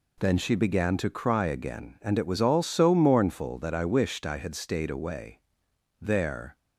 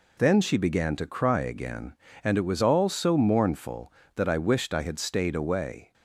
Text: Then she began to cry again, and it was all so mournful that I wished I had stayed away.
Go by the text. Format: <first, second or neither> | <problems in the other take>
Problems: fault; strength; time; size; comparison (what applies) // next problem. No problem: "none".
second | goes on to say "There"; from 6.0 s on; 0.56 s long